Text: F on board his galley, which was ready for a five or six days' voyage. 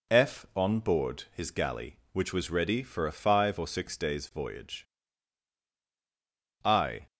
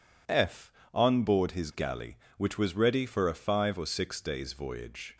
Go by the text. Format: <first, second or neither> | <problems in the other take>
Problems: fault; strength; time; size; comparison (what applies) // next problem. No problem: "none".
second | goes on to say "I"; slight; from 6.6 s on; 0.42 s long